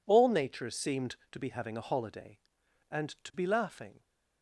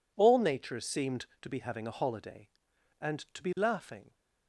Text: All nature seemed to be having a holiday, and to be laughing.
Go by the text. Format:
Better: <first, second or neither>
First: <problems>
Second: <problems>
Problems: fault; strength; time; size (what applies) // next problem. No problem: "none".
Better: neither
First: none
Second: none